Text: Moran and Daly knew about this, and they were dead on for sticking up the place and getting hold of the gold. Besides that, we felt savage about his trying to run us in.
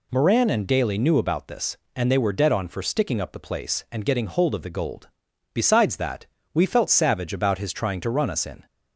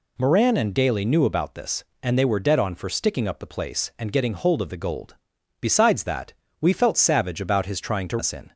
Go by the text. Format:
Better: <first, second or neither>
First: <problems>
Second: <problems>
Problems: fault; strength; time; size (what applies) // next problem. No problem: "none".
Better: first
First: none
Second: skips "run"; at 8.1 s